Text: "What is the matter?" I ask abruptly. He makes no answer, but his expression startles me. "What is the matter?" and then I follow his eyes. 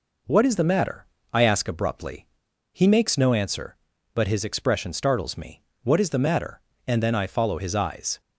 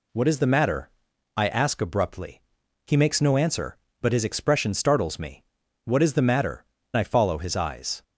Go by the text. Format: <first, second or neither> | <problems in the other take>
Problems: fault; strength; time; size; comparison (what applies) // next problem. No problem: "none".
first | skips "and then"; at 6.8 s